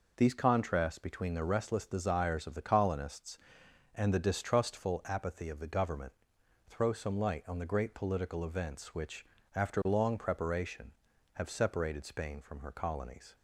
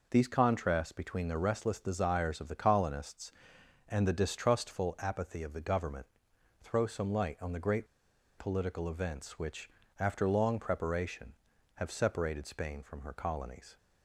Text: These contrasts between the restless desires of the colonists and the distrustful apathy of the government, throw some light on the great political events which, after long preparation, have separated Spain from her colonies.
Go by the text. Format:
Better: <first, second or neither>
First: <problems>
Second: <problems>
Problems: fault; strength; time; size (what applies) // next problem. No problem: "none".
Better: first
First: none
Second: pauses between "great" and "political"; noticeable; at 7.8 s; 0.51 s long